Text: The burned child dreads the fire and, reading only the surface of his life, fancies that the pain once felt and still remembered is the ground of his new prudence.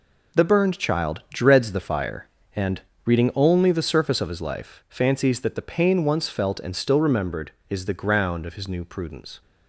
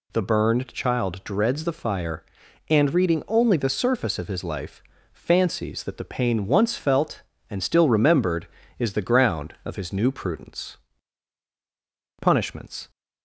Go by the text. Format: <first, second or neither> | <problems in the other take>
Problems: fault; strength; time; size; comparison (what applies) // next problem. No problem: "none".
first | goes on to say "Punishments"; noticeable; from 12.2 s on; 0.68 s long